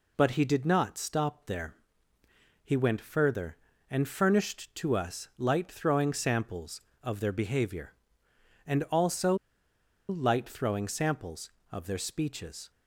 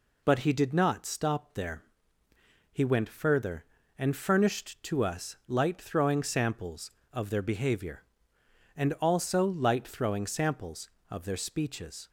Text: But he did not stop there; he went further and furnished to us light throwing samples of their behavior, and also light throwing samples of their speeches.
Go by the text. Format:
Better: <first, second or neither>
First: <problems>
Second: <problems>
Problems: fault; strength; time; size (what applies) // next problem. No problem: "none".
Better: second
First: pauses between "also" and "light"; noticeable; at 9.3 s; 0.74 s long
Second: none